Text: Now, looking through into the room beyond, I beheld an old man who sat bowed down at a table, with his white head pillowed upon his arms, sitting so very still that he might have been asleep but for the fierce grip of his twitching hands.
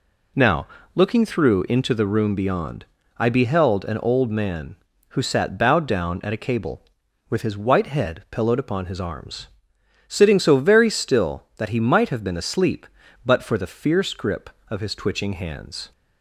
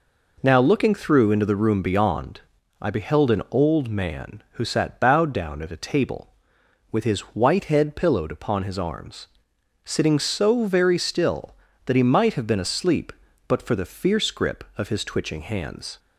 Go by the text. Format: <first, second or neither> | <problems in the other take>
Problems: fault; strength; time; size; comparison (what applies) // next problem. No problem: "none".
second | says "cable" for "table"; at 6.4 s